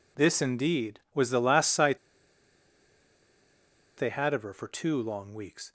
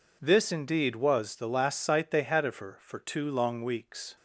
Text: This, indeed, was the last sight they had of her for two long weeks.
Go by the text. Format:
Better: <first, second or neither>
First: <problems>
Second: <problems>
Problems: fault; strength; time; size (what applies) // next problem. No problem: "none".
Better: second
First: pauses between "sight" and "they"; strong; at 1.9 s; 2.0 s long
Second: none